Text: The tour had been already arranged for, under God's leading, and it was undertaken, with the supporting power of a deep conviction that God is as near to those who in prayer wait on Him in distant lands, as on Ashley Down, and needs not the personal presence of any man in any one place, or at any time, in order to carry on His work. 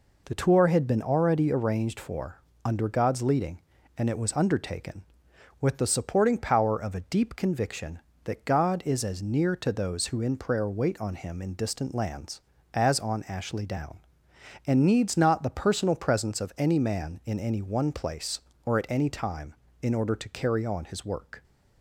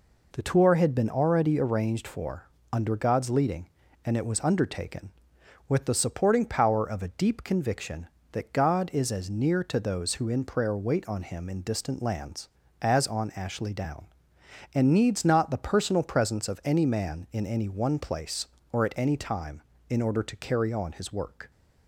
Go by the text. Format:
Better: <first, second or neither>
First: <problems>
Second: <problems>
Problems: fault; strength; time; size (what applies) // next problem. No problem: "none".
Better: neither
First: none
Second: none